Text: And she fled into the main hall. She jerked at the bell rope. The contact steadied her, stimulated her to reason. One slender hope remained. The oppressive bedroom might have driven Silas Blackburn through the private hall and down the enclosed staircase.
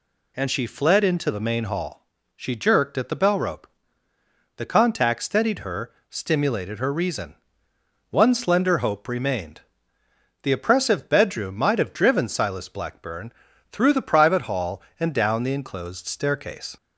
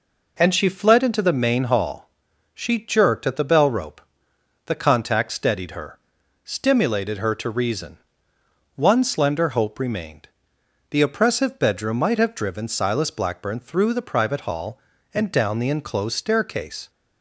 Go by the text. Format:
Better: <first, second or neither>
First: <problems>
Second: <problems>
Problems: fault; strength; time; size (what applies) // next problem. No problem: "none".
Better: second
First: skips "to"; at 6.9 s // pauses between "Blackburn" and "through"; at 13.3 s; 0.40 s long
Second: none